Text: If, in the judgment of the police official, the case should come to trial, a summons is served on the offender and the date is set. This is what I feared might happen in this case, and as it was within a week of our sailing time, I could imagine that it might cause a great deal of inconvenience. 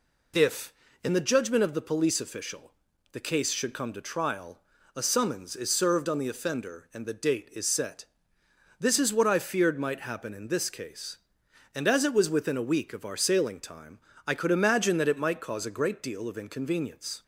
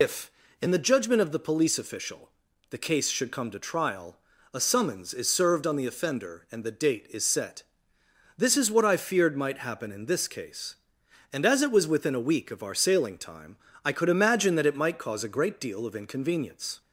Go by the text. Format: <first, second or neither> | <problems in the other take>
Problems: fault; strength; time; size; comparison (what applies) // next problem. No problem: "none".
first | loses the start of "If"; at 0.0 s; 90 ms